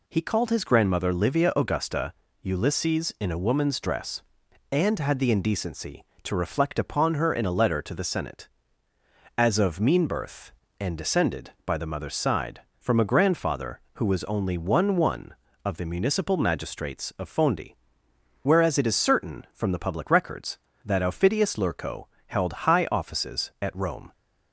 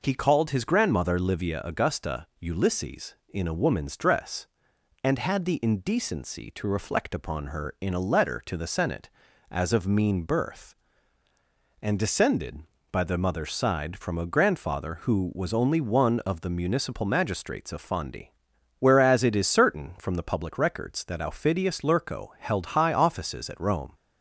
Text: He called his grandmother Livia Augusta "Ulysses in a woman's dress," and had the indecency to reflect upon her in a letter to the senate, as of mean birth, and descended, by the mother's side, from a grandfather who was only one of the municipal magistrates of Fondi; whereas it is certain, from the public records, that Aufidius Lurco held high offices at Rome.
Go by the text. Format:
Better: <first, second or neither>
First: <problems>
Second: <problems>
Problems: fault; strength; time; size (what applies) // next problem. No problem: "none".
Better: second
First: pauses between "Augusta" and "Ulysses"; slight; at 2.1 s; 0.30 s long // says "one" twice; at 14.9 s // pauses between "Lurco" and "held"; slight; at 22.0 s; 0.24 s long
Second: none